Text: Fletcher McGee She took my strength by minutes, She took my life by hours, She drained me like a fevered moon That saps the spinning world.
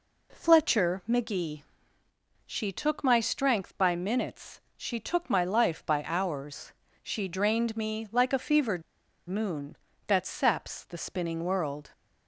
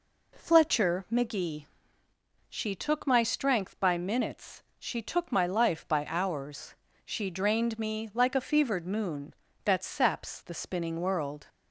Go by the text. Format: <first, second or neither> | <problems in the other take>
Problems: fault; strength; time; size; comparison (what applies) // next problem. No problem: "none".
second | pauses between "McGee" and "She"; noticeable; at 1.6 s; 0.84 s long; noticeable in the second // pauses between "fevered" and "moon"; noticeable; at 8.8 s; 0.47 s long